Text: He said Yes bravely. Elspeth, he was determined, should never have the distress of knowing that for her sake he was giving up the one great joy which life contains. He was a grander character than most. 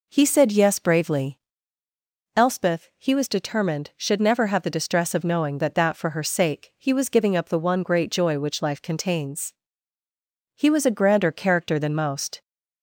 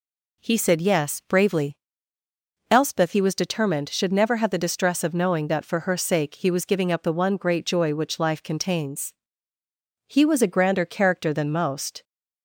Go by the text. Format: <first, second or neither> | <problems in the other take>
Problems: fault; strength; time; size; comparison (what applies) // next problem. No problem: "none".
second | says "that" twice; at 5.7 s